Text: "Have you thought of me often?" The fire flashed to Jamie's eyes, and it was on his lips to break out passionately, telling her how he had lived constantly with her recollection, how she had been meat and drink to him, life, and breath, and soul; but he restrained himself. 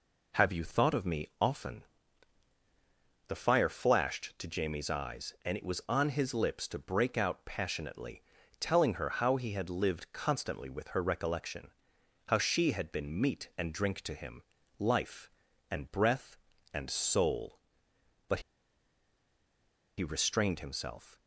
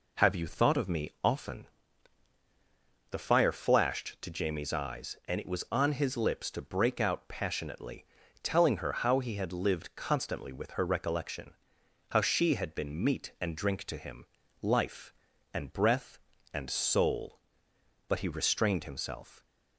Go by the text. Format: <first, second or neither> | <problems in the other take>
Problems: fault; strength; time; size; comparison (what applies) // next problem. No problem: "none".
second | pauses between "but" and "he"; strong; at 18.3 s; 1.5 s long